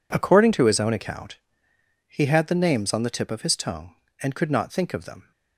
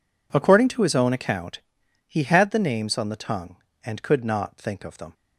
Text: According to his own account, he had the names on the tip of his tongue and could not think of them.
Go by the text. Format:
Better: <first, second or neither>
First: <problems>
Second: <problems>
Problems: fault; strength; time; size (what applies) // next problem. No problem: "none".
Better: first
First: none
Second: skips "tip of his"; at 3.1 s